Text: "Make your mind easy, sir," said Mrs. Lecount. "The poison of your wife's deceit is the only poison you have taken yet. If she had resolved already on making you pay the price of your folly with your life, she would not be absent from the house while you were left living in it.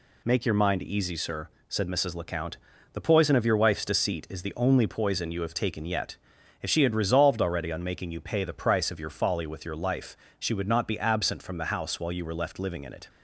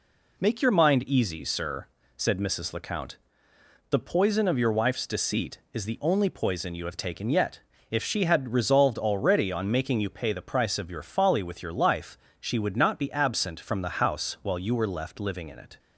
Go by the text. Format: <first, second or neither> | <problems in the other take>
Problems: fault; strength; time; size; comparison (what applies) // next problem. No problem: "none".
neither | none